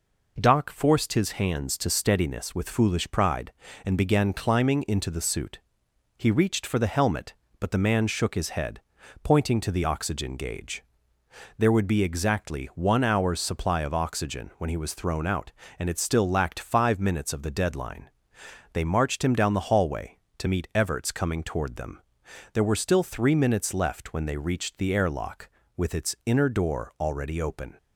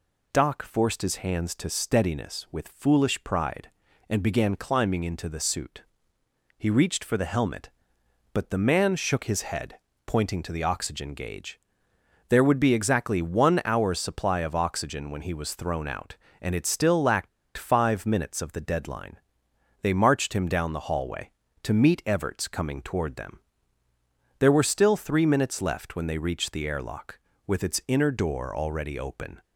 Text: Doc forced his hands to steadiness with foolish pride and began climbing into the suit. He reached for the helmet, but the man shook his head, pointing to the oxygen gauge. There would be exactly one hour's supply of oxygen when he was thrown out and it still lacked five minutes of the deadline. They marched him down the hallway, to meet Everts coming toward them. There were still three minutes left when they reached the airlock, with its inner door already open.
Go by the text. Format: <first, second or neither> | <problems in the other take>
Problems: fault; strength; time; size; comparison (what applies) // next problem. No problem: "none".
first | pauses between "lacked" and "five"; slight; at 17.2 s; 0.28 s long